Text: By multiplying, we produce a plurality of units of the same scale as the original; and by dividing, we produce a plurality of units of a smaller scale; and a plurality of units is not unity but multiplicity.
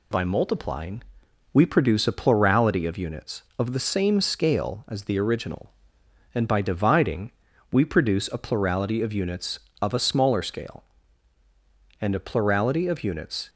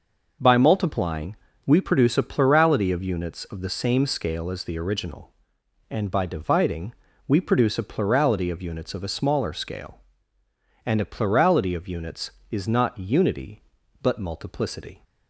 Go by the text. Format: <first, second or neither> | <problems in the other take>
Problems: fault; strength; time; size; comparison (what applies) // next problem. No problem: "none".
second | stops before "is not unity but multiplicity"; at 13.4 s